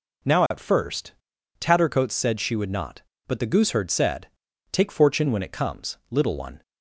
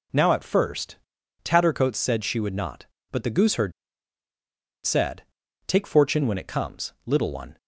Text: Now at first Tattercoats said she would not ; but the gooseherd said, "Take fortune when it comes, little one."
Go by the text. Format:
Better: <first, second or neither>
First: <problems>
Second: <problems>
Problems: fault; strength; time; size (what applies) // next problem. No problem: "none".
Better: first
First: pauses between "first" and "Tattercoats"; noticeable; at 1.1 s; 0.48 s long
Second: pauses between "first" and "Tattercoats"; noticeable; at 0.9 s; 0.48 s long // pauses between "gooseherd" and "said"; at 3.7 s; 1.1 s long